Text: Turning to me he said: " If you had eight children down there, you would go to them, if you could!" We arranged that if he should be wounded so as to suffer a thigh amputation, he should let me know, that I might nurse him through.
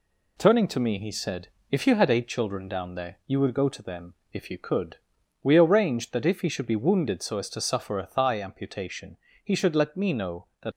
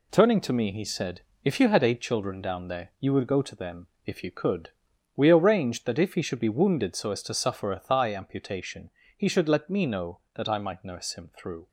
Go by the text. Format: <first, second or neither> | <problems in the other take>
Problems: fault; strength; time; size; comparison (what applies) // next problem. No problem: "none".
second | stops before "I might nurse him through"; at 10.7 s